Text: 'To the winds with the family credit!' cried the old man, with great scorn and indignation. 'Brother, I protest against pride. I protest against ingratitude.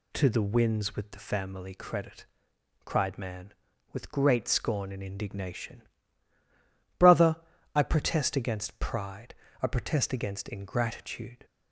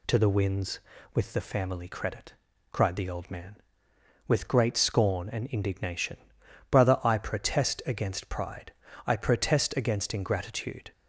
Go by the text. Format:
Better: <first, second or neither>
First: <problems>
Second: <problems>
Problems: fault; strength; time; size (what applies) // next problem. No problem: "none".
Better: second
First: skips "the old"; at 3.1 s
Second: none